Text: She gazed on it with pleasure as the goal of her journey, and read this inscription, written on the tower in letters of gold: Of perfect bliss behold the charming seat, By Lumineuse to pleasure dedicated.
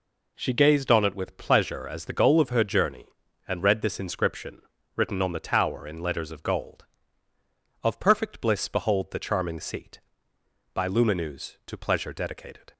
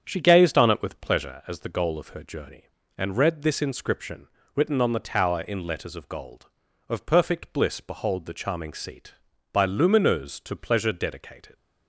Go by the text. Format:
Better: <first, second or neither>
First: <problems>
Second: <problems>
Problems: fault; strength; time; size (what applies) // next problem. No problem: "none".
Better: first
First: none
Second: starts louder than the rest; strong; until 1.5 s; 8 dB